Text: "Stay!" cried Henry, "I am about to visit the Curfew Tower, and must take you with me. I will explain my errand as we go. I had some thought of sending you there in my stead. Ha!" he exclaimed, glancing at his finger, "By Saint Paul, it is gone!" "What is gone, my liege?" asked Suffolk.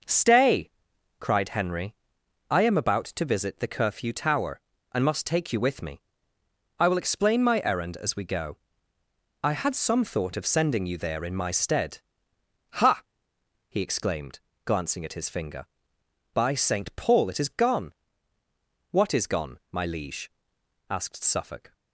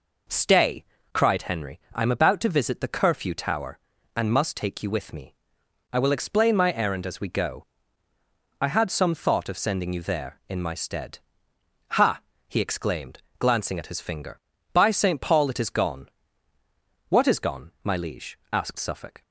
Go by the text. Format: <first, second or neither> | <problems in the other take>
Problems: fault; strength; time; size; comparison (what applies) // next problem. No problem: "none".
neither | none